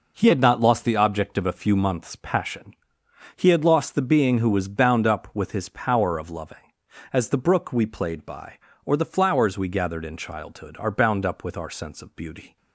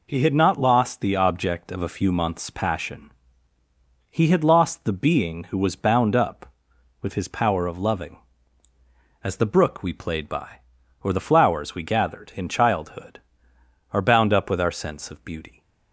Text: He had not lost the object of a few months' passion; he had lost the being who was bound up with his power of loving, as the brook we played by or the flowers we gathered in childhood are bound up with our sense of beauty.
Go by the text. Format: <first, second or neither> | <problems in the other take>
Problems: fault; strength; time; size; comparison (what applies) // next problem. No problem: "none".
neither | none